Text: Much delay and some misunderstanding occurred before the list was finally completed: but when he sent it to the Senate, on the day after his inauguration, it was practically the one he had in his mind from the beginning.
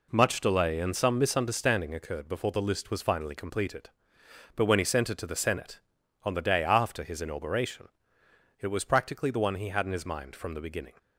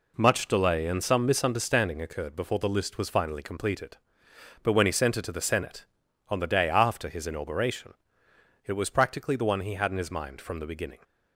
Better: neither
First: none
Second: none

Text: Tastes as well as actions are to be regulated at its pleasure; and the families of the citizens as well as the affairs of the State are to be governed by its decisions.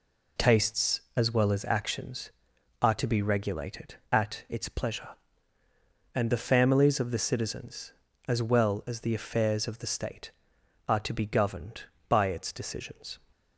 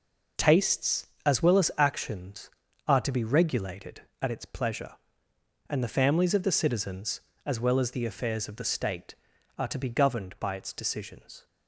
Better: neither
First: none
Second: none

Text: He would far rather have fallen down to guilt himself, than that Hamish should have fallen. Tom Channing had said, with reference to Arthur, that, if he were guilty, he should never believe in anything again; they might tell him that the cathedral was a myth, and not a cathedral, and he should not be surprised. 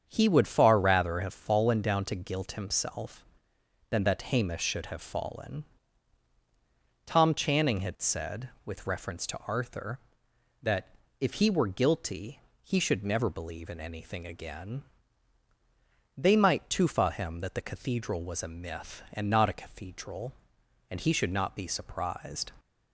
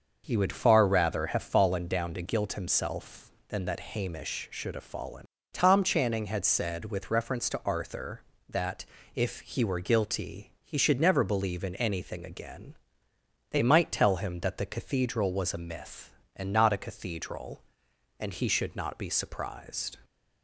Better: second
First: starts louder than the rest; strong; until 1.0 s; 7.5 dB // says "tufa" for "tell"; at 16.6 s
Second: starts louder than the rest; noticeable; until 1.2 s; 6 dB

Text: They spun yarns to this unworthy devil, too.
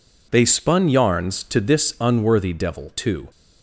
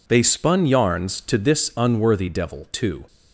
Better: neither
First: none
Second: none

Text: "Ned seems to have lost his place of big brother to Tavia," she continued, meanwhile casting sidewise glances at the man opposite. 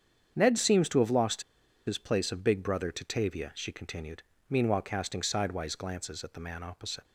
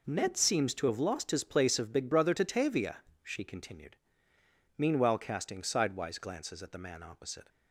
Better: second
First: starts louder than the rest; strong; until 1.3 s; 8 dB // pauses between "lost" and "his"; at 1.4 s; 0.44 s long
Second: none

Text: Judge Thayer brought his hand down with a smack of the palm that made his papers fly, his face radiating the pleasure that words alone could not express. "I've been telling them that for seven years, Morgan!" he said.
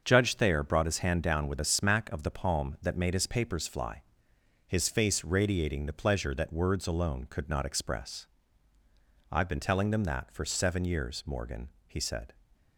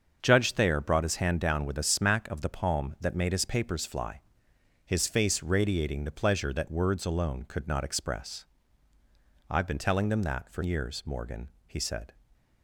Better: first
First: starts louder than the rest; until 1.0 s; 6.5 dB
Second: starts louder than the rest; until 1.2 s; 6.5 dB // skips "seven"; at 10.6 s

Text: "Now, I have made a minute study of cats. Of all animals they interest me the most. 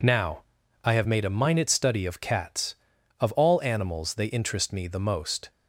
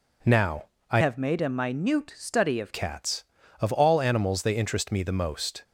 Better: first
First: none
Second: changes voice from "have" to "of"; from 1.0 to 2.7 s; 1.7 s long

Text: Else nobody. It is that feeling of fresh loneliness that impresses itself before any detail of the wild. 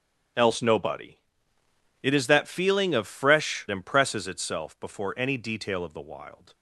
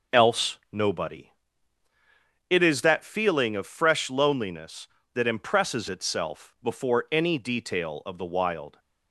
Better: second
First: starts louder than the rest; strong; until 2.2 s; 8 dB // skips "loneliness that"; at 3.6 s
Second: none

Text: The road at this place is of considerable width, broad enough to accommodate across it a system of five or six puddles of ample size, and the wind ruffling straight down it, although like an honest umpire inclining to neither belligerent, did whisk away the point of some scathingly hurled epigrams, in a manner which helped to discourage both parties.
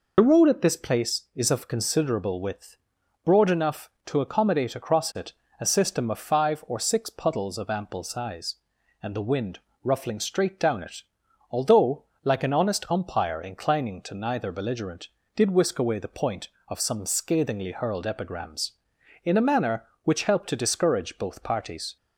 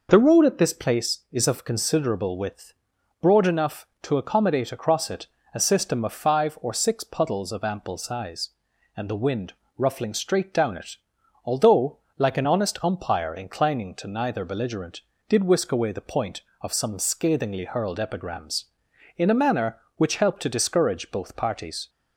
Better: second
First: loses the start of "The"; at 0.1 s; 55 ms // pauses between "it" and "a"; slight; at 5.3 s; 0.26 s long // pauses between "wind" and "ruffling"; slight; at 9.5 s; 0.26 s long // pauses between "although" and "like"; slight; at 12.0 s; 0.20 s long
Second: pauses between "it" and "a"; slight; at 5.2 s; 0.26 s long // pauses between "wind" and "ruffling"; slight; at 9.5 s; 0.26 s long // pauses between "although" and "like"; slight; at 11.9 s; 0.20 s long

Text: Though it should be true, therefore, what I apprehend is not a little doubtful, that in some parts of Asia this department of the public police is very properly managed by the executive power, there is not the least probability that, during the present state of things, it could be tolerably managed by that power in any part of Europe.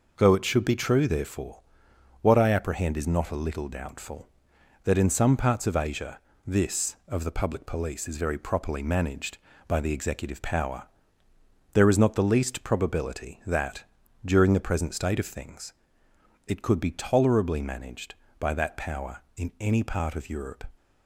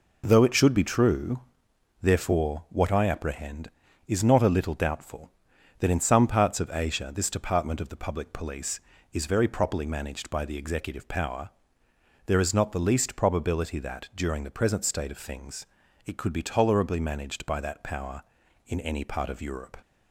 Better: second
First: pauses between "Asia" and "this"; slight; at 6.1 s; 0.28 s long // skips "department"; at 7.0 s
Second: none

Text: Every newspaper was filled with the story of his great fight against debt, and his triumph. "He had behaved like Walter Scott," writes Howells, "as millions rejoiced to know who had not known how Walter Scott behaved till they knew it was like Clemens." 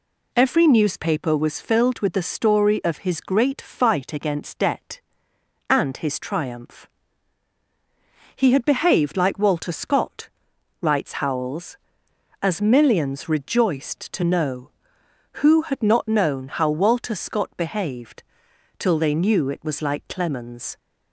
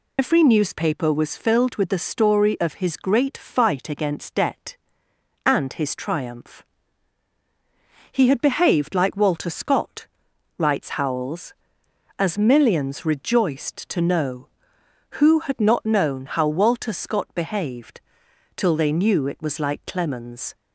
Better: first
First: pauses between "behaved" and "till"; noticeable; at 18.2 s; 0.56 s long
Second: loses the start of "Every"; at 0.1 s; 90 ms // pauses between "behaved" and "till"; noticeable; at 17.9 s; 0.56 s long

